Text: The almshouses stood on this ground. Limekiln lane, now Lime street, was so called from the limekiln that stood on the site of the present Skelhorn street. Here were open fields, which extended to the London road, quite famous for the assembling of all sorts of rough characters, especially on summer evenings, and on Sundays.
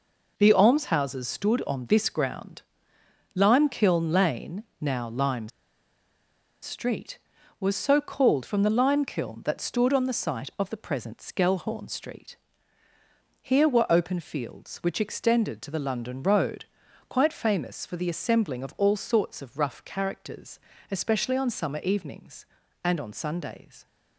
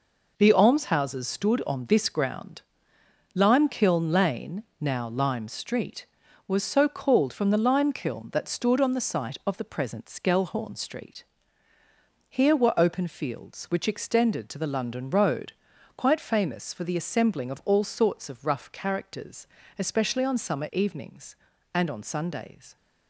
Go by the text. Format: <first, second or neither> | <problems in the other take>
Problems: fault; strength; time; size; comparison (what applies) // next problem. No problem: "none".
second | pauses between "Lime" and "street"; at 5.4 s; 1.1 s long